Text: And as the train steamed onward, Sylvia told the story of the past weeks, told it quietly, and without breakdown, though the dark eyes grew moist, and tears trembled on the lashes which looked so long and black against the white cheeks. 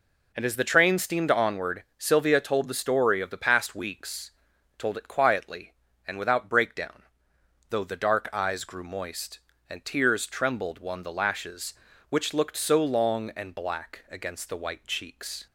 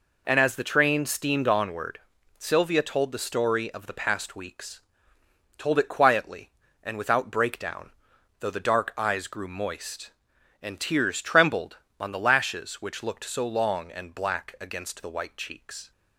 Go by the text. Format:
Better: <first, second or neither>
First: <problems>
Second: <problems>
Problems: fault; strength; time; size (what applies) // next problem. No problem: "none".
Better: second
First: says "one" for "on"; at 10.7 s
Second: none